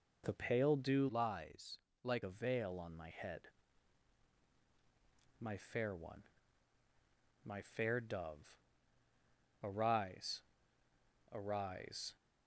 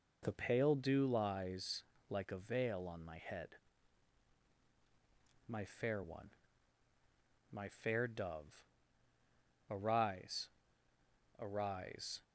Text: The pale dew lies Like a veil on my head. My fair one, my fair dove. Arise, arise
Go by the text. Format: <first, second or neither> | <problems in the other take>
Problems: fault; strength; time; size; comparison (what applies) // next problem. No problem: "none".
second | changes voice from "lies" to "Like"; from 1.0 to 2.2 s; 1.2 s long // pauses between "lies" and "Like"; slight; at 1.7 s; 0.22 s long; slight in the second